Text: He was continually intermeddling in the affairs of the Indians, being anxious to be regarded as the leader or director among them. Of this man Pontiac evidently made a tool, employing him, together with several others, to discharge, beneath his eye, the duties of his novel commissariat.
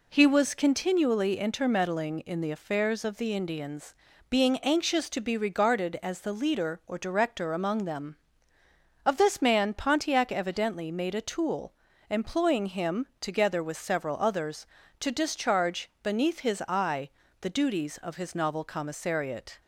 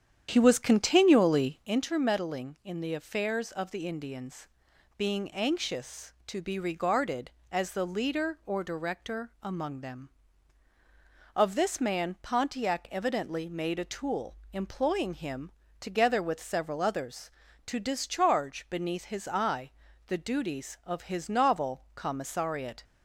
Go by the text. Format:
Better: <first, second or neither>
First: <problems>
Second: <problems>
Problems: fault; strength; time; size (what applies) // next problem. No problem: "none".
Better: first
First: none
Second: starts louder than the rest; strong; until 1.7 s; 9 dB